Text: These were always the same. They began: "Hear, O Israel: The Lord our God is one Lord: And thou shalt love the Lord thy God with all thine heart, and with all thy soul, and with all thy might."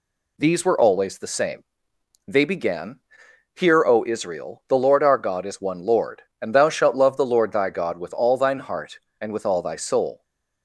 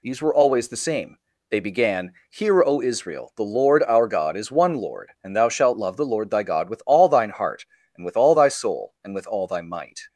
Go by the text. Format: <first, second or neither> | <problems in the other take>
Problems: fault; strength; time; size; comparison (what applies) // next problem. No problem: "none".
second | stops before "and with all thy might"; at 10.2 s